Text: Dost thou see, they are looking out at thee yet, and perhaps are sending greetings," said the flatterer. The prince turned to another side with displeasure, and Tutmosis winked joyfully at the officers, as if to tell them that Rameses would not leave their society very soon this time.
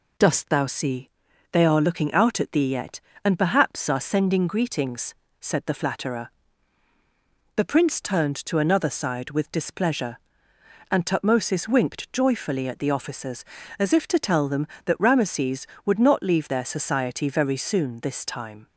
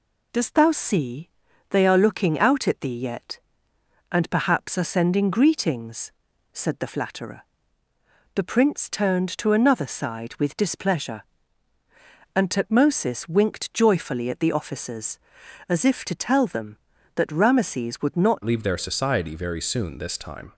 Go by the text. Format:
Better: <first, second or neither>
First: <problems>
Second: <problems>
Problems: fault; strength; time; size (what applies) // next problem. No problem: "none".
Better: first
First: none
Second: changes voice at "leave"; from 18.4 s on; 2.1 s long